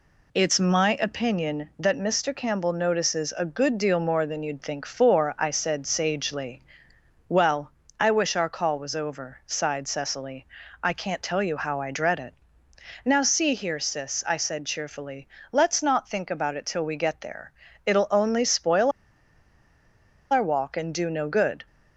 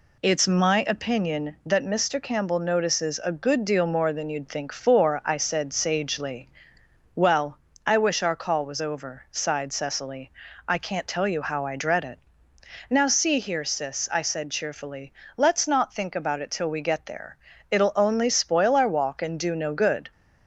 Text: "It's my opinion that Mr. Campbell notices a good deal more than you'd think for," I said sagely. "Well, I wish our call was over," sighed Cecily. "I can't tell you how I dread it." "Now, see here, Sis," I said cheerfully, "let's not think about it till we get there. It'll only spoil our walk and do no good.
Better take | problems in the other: second | pauses between "spoil" and "our"; strong; at 18.9 s; 1.4 s long

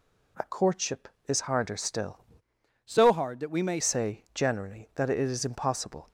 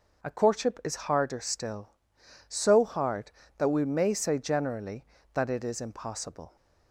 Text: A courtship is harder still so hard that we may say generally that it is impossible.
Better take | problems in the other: second | changes voice from "so" to "may"; from 2.8 to 3.8 s; 1.0 s long

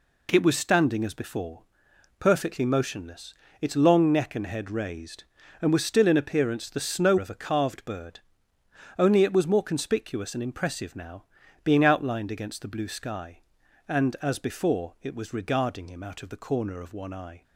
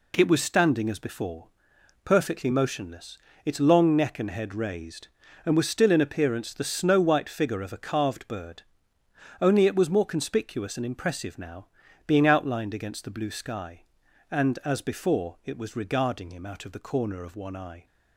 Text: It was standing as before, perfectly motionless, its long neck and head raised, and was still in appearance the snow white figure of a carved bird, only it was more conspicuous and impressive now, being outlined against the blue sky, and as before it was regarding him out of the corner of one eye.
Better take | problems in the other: second | skips "white figure"; at 7.1 s

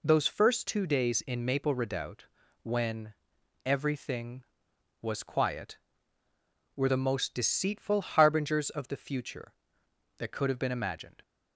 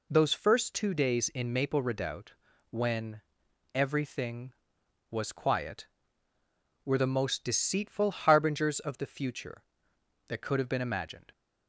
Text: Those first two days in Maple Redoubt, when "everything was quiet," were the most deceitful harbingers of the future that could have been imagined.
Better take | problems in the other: neither | pauses between "when" and "everything"; noticeable; the same in both

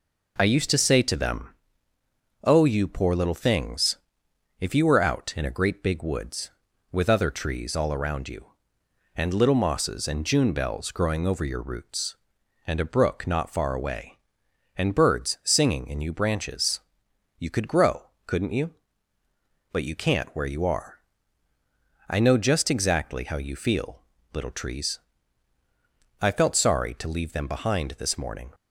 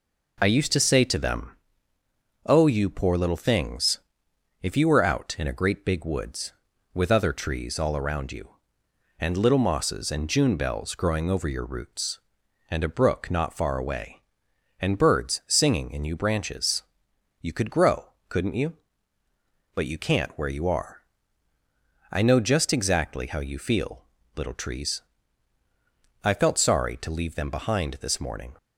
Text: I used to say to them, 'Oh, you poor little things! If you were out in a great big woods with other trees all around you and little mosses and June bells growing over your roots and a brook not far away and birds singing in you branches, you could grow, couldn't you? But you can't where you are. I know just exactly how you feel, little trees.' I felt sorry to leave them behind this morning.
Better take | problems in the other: neither | none

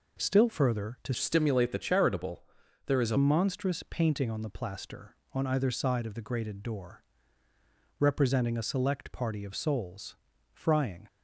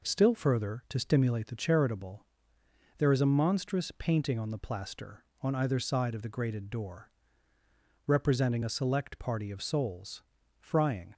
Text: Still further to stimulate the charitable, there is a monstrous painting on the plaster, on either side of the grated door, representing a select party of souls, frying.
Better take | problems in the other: second | changes voice from "stimulate" to "a"; from 1.1 to 3.1 s; 2.0 s long

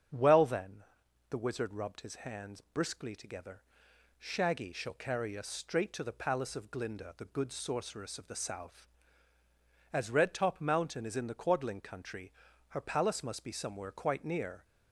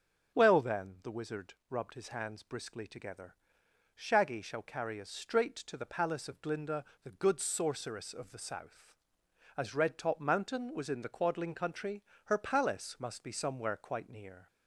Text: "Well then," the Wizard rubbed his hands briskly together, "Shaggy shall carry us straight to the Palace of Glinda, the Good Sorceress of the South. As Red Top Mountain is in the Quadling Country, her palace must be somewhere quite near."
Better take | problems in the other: first | starts louder than the rest; until 1.4 s; 7 dB; strong in the first // pauses between "Wizard" and "rubbed"; slight; at 1.5 s; 0.16 s long // says "was" for "is"; at 10.7 s

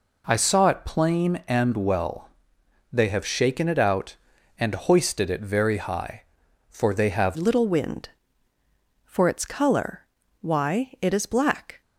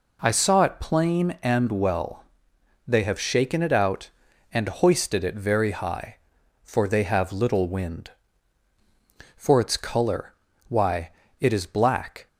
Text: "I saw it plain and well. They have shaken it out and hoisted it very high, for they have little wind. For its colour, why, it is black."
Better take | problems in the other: second | changes voice at "little"; from 7.3 s on; 4.5 s long

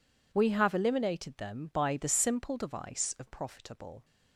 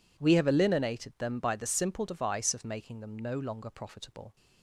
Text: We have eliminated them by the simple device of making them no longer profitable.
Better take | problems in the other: second | skips "making them no longer"; at 3.2 s

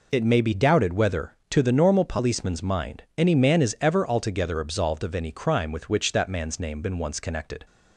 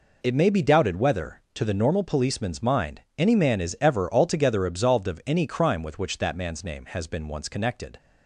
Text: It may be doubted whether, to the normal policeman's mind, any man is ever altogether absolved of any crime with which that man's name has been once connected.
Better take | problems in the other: second | skips "has"; at 6.8 s

